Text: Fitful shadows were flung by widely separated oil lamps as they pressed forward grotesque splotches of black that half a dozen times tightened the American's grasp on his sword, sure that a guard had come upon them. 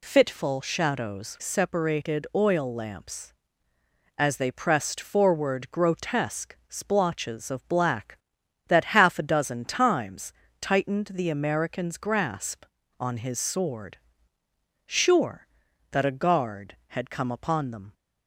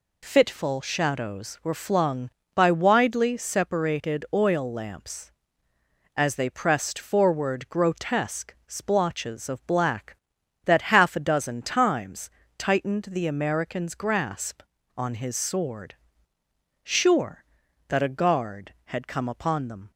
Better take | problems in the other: second | skips "were flung by widely"; at 1.3 s // pauses between "times" and "tightened"; slight; at 10.3 s; 0.26 s long; slight in the second

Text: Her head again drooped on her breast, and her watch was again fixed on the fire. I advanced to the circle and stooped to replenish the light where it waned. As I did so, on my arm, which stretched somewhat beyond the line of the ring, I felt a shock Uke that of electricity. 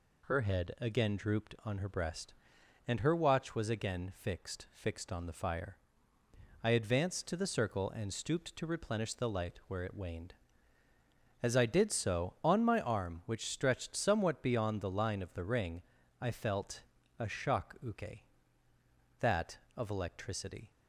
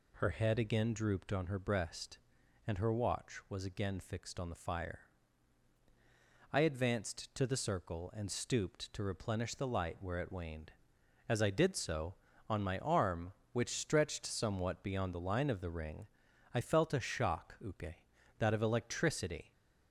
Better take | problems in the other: second | says "fixed" twice; at 4.7 s // pauses between "felt" and "a"; at 16.8 s; 0.38 s long

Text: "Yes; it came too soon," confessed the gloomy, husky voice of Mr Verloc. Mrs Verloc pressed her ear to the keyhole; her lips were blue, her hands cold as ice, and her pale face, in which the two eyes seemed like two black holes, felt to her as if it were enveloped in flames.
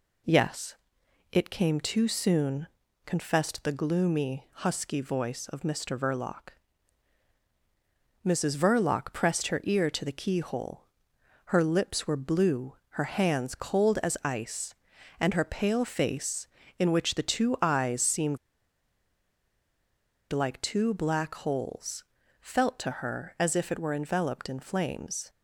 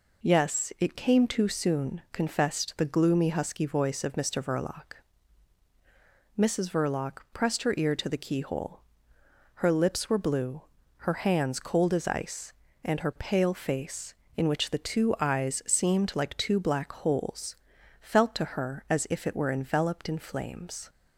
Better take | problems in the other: second | pauses between "seemed" and "like"; strong; at 18.3 s; 1.9 s long

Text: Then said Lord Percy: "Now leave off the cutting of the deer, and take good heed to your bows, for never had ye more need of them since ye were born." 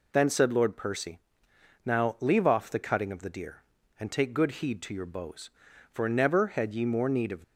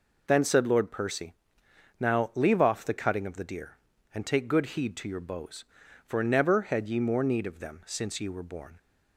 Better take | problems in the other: second | stops before "them since ye were born"; at 7.4 s

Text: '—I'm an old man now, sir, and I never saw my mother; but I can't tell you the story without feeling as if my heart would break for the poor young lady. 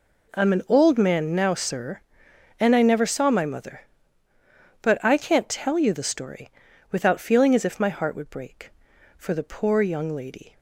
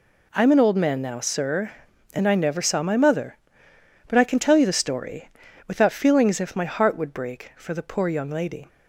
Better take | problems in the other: first | says "can" for "can't"; at 4.2 s // pauses between "story" and "without"; at 5.2 s; 0.38 s long; also in the first

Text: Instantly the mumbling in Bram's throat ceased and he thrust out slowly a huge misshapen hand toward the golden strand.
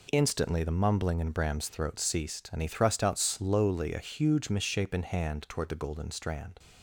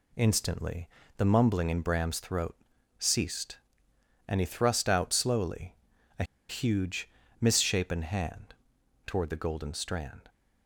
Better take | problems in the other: first | pauses between "Instantly" and "the"; slight; at 0.8 s; 0.30 s long // pauses between "throat" and "ceased"; at 2.5 s; 0.44 s long // pauses between "slowly" and "a"; noticeable; at 5.7 s; 0.46 s long // pauses between "a" and "huge"; slight; at 6.2 s; 0.25 s long // pauses between "huge" and "misshapen"; slight; at 7.0 s; 0.32 s long // pauses between "hand" and "toward"; noticeable; at 8.5 s; 0.52 s long

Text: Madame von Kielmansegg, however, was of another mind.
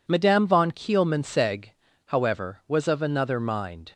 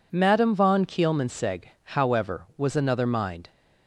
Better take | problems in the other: first | skips "of"; at 2.7 s

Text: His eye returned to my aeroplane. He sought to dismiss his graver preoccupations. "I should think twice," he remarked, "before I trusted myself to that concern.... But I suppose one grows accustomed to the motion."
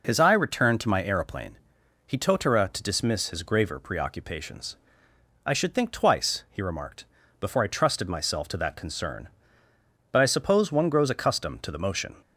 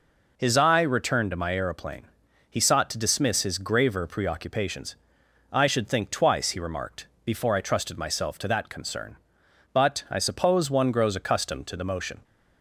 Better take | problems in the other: second | says "totara" for "sought"; at 2.1 s

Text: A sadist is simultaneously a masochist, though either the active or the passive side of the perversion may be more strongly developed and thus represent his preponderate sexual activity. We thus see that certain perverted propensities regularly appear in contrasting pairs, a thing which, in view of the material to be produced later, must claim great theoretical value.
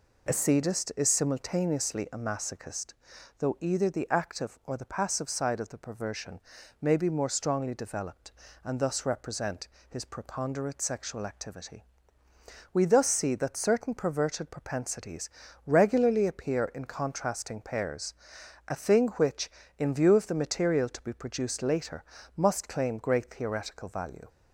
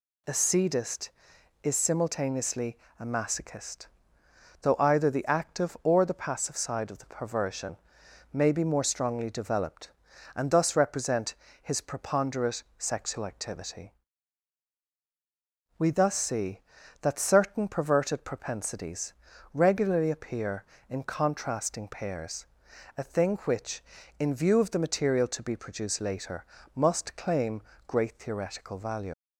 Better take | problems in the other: first | pauses between "simultaneously" and "a"; slight; at 2.7 s; 0.24 s long // pauses between "perversion" and "may"; noticeable; at 7.7 s; 0.54 s long; also in the first // pauses between "represent" and "his"; slight; at 11.3 s; 0.28 s long; slight in the first // pauses between "preponderate" and "sexual"; slight; at 12.6 s; 0.16 s long // pauses between "propensities" and "regularly"; at 19.1 s; 0.40 s long; slight in the first // pauses between "claim" and "great"; slight; at 27.6 s; 0.26 s long // leaves "value" unfinished; at 29.1 s; 60 ms

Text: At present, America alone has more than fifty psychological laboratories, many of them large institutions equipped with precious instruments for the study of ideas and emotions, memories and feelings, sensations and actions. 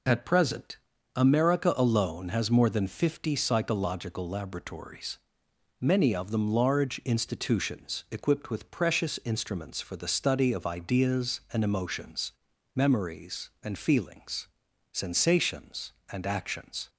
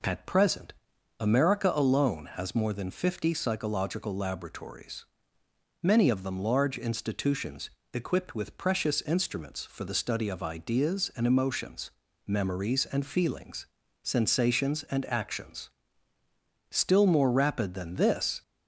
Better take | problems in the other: first | pauses between "institutions" and "equipped"; slight; at 7.6 s; 0.24 s long // goes on to say "Still more rapid than this"; strong; from 16.7 s on; 1.7 s long

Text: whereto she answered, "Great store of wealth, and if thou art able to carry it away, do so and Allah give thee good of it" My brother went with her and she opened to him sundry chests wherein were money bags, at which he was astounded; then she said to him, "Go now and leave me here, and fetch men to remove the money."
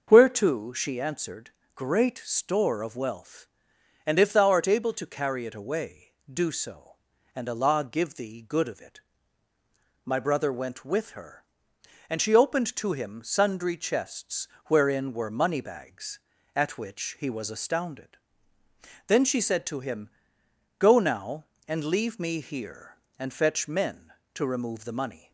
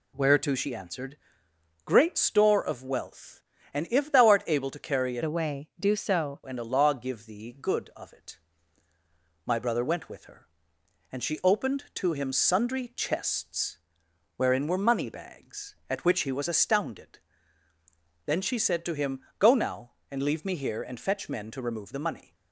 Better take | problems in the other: first | changes voice from "away" to "so"; from 5.2 to 6.4 s; 1.2 s long // pauses between "it" and "My"; at 8.3 s; 1.0 s long; also in the first // pauses between "chests" and "wherein"; noticeable; at 13.7 s; 0.60 s long; slight in the first

